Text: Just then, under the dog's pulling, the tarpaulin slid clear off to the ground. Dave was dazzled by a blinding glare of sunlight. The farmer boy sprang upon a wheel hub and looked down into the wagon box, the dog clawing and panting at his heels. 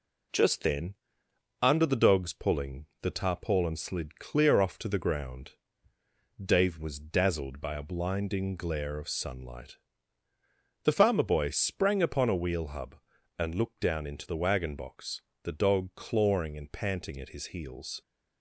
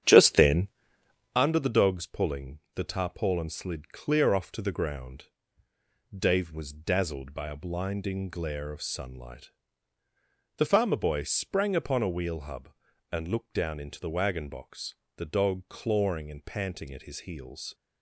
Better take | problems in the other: first | starts louder than the rest; strong; until 1.4 s; 9 dB

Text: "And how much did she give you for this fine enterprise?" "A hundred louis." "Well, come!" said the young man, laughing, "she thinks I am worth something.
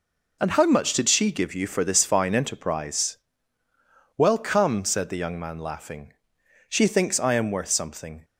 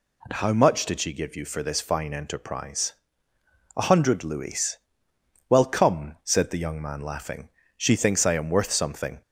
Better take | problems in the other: second | skips "A hundred louis"; at 3.6 s

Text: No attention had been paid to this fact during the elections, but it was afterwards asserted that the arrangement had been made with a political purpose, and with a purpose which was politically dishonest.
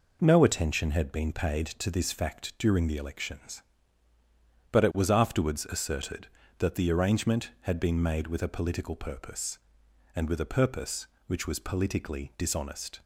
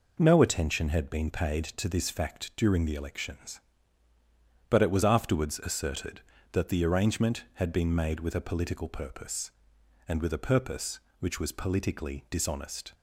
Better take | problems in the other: neither | none

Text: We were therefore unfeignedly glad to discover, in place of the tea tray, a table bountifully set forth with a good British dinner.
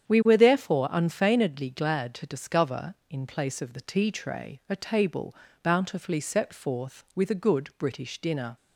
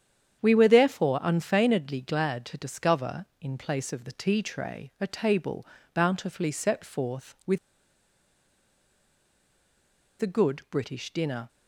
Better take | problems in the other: first | starts louder than the rest; strong; until 1.4 s; 8.5 dB; strong in the first // pauses between "table" and "bountifully"; slight; at 5.6 s; 0.26 s long; slight in the first // pauses between "with" and "a"; strong; at 7.5 s; 2.6 s long

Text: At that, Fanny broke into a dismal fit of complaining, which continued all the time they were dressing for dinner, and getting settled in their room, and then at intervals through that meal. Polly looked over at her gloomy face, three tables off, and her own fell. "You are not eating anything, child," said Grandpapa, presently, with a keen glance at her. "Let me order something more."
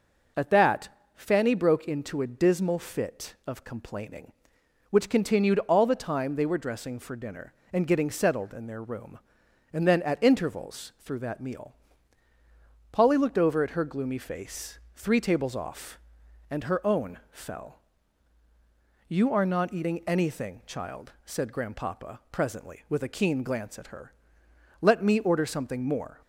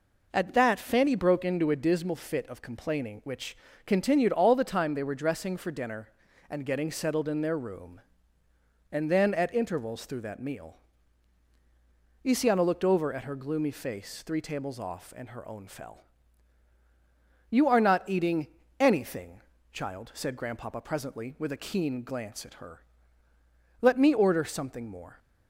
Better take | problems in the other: first | pauses between "which" and "continued"; slight; at 3.5 s; 0.30 s long // says "Isiana" for "Polly"; at 12.2 s // pauses between "eating" and "anything"; slight; at 18.4 s; 0.34 s long

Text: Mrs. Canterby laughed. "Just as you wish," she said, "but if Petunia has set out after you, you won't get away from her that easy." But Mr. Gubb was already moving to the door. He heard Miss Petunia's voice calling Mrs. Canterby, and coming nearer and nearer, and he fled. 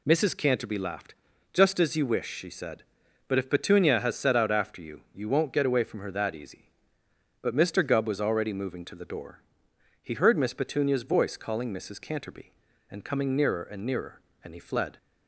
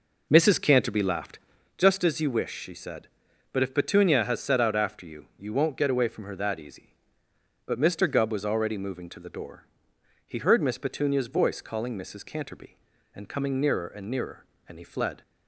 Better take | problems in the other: first | starts louder than the rest; noticeable; until 1.7 s; 4.5 dB

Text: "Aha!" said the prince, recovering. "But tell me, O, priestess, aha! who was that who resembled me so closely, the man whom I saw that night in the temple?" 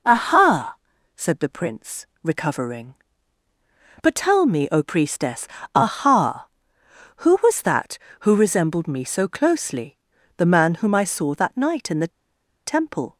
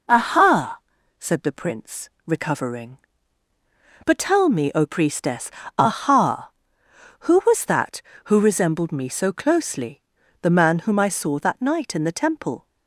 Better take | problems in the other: second | pauses between "the" and "temple"; noticeable; at 12.1 s; 0.57 s long

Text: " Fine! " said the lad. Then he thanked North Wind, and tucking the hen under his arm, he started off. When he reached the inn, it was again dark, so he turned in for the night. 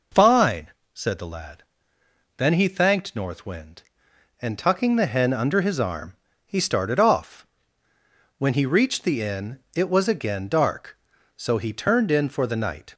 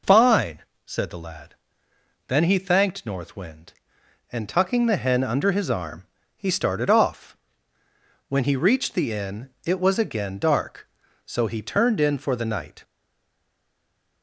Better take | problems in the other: first | stays silent after the last word; noticeable; from 12.8 s on; 1.4 s long

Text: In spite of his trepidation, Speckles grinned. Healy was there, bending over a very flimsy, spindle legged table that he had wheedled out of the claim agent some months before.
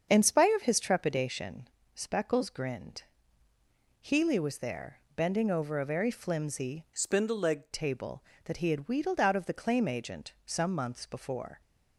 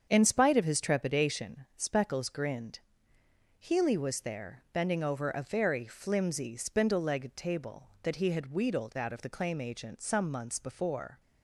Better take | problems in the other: second | starts louder than the rest; until 1.1 s; 7 dB; strong in the second // changes voice from "spindle" to "legged"; from 6.9 to 7.7 s; 0.8 s long

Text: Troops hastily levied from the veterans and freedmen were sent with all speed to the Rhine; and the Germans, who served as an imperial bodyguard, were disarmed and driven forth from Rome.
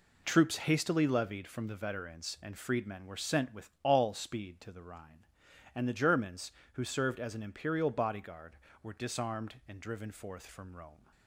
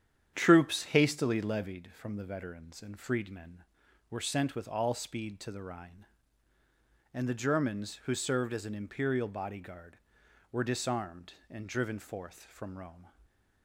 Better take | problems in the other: first | starts louder than the rest; strong; until 1.8 s; 9 dB // stays silent after the last word; slight; from 13.0 s on; 0.6 s long

